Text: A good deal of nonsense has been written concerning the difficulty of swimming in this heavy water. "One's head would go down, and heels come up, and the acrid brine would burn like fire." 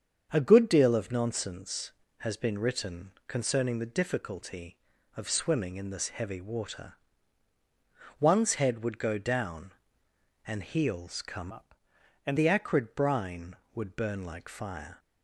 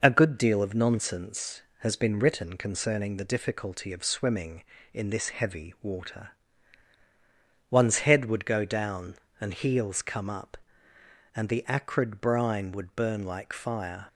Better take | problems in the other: second | starts louder than the rest; strong; until 1.3 s; 7 dB // changes voice from "up" to "and"; from 11.5 to 12.3 s; 0.8 s long

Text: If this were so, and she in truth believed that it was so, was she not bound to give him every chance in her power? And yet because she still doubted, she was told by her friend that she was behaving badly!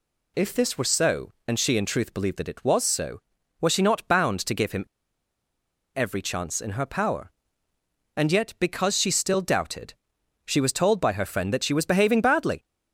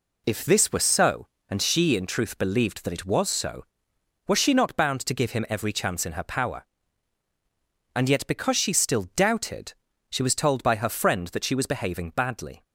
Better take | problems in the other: second | pauses between "him" and "every"; at 4.8 s; 1.0 s long

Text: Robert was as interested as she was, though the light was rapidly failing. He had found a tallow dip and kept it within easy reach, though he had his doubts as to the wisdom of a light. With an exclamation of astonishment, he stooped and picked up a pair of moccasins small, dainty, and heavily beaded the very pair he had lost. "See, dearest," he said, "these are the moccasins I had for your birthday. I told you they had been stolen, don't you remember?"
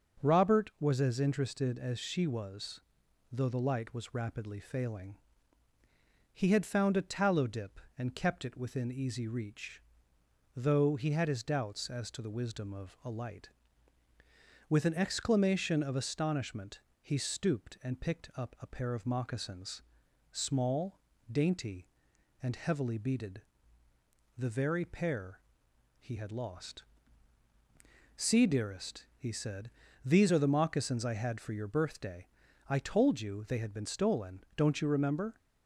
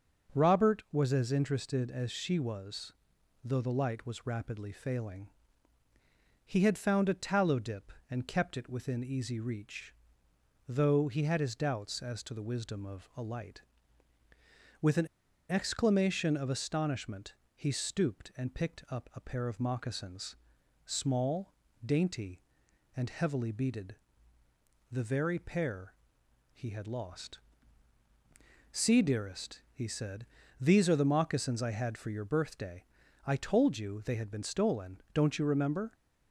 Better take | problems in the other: first | starts louder than the rest; until 1.4 s; 6 dB; also in the first // pauses between "an" and "exclamation"; at 15.0 s; 0.42 s long // pauses between "moccasins" and "small"; noticeable; at 20.3 s; 0.48 s long; noticeable in the first // pauses between "beaded" and "the"; noticeable; at 23.9 s; 0.94 s long; noticeable in the first // pauses between "pair" and "he"; noticeable; at 25.9 s; 0.58 s long; noticeable in the first

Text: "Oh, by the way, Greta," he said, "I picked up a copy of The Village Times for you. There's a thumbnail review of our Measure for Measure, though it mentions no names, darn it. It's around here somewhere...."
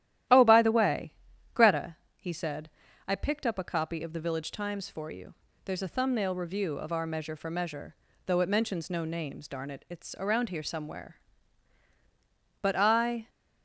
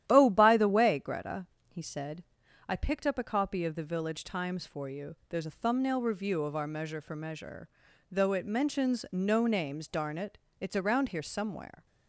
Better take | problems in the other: second | starts louder than the rest; strong; until 1.7 s; 12.5 dB; strong in the second // goes on to say "But I"; noticeable; from 12.6 s on; 0.68 s long

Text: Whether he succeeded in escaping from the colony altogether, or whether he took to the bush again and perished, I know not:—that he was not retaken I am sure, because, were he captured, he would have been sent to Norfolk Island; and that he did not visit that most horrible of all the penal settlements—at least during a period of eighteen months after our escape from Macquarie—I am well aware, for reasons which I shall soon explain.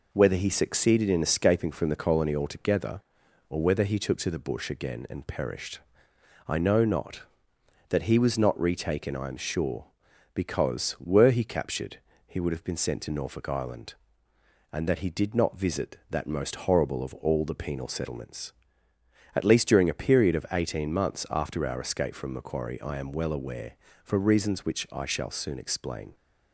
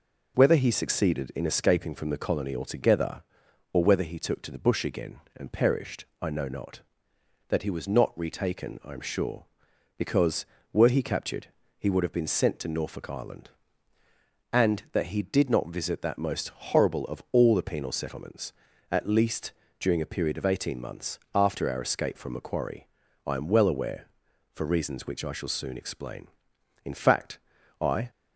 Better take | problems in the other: first | pauses between "least" and "during"; slight; at 19.5 s; 0.26 s long // pauses between "months" and "after"; slight; at 21.1 s; 0.16 s long // goes on to say "In fact I"; noticeable; from 26.8 s on; 1.2 s long

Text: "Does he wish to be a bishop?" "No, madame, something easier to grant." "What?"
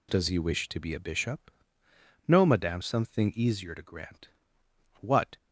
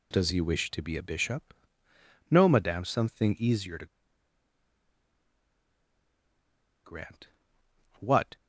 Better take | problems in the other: first | pauses between "to" and "grant"; strong; at 3.8 s; 2.9 s long

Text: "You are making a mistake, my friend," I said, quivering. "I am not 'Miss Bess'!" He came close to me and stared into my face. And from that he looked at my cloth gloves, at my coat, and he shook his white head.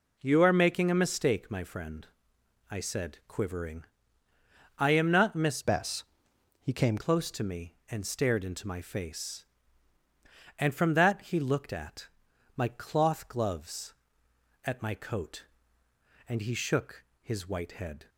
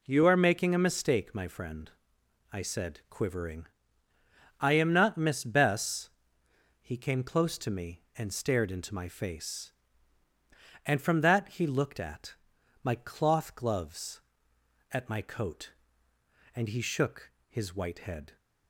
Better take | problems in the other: second | changes voice from "Bess" to "came"; from 5.6 to 6.9 s; 1.3 s long // pauses between "at" and "my"; noticeable; at 12.0 s; 0.46 s long; noticeable in the second // pauses between "shook" and "his"; slight; at 17.0 s; 0.20 s long; slight in the second

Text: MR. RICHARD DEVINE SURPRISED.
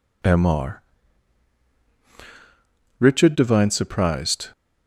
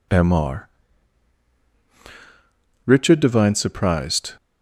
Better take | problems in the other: neither | none

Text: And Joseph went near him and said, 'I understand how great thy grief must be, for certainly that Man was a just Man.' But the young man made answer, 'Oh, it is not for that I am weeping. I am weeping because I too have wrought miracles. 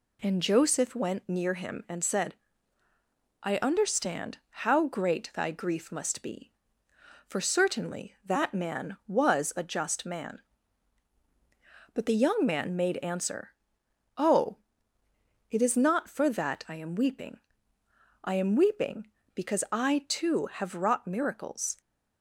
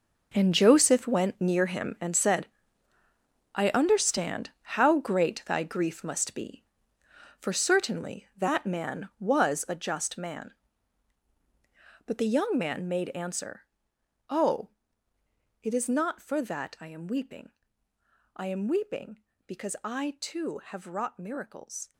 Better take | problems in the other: first | gets quieter; strong; throughout; 13.5 dB

